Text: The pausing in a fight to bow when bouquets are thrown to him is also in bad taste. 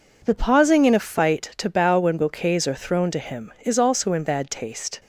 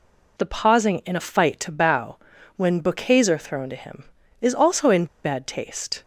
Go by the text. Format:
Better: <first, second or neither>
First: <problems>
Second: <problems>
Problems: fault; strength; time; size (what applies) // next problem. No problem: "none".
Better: first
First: none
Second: pauses between "bow" and "when"; at 2.1 s; 0.40 s long // pauses between "in" and "bad"; slight; at 5.0 s; 0.17 s long